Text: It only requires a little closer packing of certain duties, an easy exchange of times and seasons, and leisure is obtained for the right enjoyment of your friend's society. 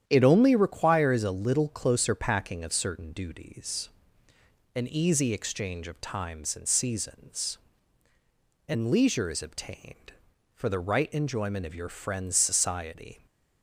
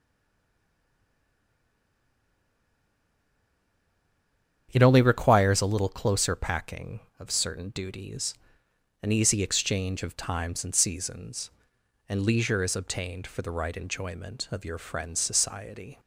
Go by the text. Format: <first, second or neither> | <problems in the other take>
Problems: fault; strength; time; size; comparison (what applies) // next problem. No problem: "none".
first | stays silent before the first word; strong; until 4.6 s; 4.6 s long // starts louder than the rest; strong; until 5.7 s; 8.5 dB; strong in the first